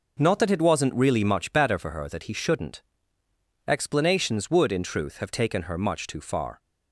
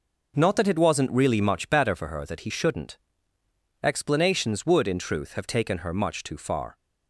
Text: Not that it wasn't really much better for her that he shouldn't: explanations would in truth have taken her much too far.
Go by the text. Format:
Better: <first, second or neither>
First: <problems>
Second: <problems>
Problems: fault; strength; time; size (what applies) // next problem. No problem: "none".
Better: neither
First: none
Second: none